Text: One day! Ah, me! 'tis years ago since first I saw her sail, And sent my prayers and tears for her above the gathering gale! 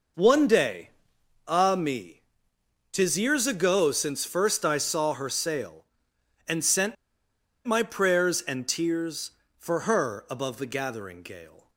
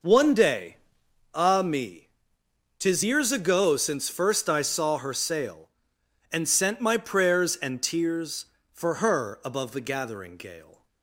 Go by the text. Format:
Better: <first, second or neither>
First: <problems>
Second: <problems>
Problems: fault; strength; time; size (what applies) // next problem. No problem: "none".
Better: second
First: pauses between "sent" and "my"; noticeable; at 6.9 s; 0.69 s long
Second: none